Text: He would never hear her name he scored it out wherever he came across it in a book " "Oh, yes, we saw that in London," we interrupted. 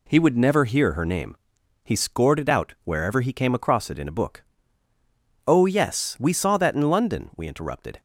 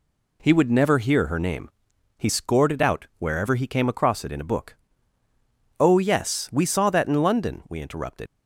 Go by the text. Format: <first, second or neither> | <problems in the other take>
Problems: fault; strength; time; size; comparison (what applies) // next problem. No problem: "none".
first | pauses between "name" and "he"; noticeable; at 1.6 s; 0.48 s long; noticeable in the first // leaves "interrupted" unfinished; at 8.2 s; 80 ms